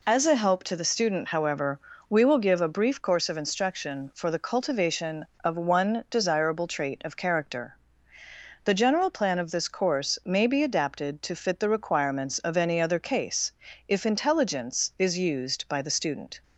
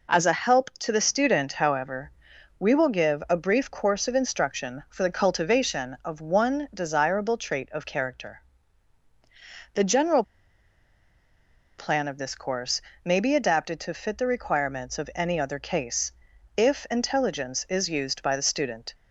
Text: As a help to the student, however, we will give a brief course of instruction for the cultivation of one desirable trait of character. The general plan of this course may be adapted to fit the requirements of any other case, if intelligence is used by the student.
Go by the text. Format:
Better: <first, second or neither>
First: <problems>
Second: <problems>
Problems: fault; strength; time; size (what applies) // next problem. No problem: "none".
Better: first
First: none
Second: pauses between "general" and "plan"; strong; at 10.2 s; 1.5 s long // pauses between "course" and "may"; slight; at 12.8 s; 0.24 s long